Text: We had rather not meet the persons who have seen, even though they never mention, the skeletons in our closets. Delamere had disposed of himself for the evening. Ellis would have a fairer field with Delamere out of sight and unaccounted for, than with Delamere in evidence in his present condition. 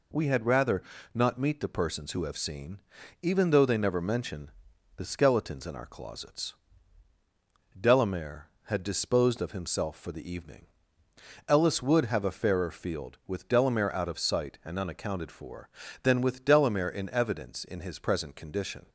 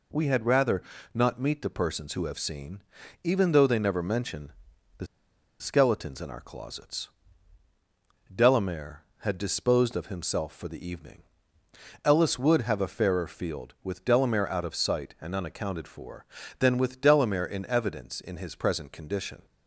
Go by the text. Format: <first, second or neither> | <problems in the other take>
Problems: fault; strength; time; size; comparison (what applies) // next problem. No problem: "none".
first | pauses between "rather" and "not"; slight; at 0.8 s; 0.32 s long; slight in the first // pauses between "the" and "skeletons"; noticeable; at 5.0 s; 0.54 s long